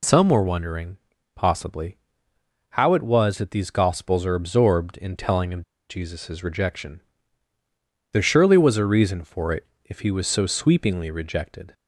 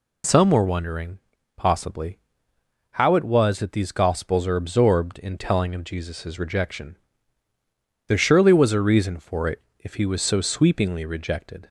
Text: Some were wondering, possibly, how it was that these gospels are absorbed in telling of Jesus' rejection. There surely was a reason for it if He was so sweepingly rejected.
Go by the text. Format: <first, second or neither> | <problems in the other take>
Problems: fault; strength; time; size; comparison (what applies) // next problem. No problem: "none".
second | pauses between "of" and "Jesus"; slight; at 5.6 s; 0.27 s long // pauses between "it" and "if"; slight; at 9.6 s; 0.20 s long; slight in the second